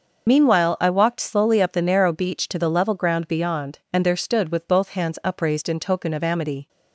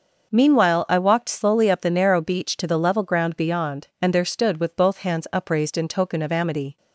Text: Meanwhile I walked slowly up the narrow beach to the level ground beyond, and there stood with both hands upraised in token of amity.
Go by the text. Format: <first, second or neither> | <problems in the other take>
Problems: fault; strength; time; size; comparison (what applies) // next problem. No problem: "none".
second | loses the start of "Meanwhile"; at 0.2 s; 50 ms // starts louder than the rest; noticeable; until 1.3 s; 6 dB; noticeable in the second